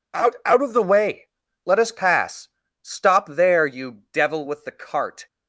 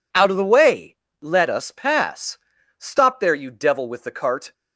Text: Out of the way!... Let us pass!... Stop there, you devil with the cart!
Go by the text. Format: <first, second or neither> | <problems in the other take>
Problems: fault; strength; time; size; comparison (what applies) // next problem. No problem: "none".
second | says "Out" twice; at 0.4 s